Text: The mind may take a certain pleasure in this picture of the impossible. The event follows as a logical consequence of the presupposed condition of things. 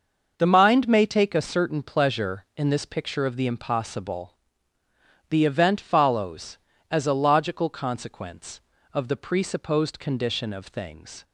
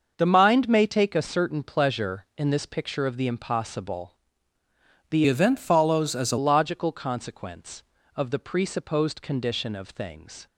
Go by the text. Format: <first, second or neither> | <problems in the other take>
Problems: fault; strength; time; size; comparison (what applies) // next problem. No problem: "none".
first | starts louder than the rest; until 1.1 s; 6.5 dB; also in the first // changes voice from "event" to "a"; from 5.2 to 6.3 s; 1.1 s long